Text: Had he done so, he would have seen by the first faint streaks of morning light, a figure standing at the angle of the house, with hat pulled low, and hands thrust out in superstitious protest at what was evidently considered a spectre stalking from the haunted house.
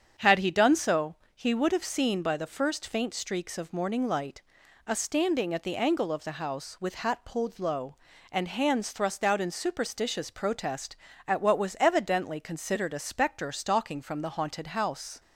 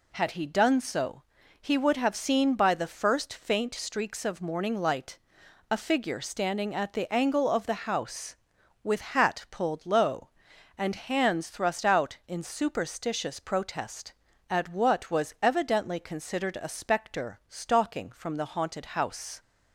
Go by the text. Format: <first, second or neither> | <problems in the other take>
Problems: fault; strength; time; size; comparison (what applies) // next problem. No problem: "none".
second | starts louder than the rest; strong; until 1.3 s; 8 dB // skips "figure"; at 4.9 s